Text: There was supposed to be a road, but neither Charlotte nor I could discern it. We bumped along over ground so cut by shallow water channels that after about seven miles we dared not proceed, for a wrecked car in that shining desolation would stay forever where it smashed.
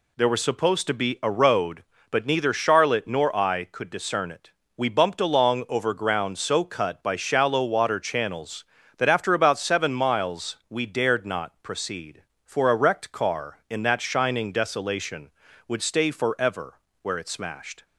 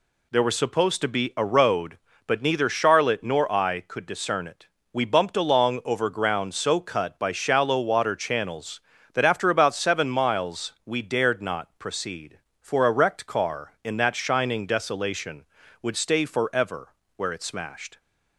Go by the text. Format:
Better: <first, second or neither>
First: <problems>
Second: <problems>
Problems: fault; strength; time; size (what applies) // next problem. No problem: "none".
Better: neither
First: pauses between "forever" and "where"; slight; at 16.7 s; 0.24 s long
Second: pauses between "forever" and "where"; slight; at 16.9 s; 0.24 s long